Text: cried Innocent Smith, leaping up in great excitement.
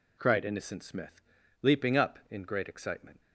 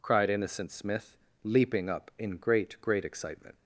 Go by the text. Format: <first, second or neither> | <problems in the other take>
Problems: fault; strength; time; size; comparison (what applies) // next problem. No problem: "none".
first | says "great" twice; at 2.8 s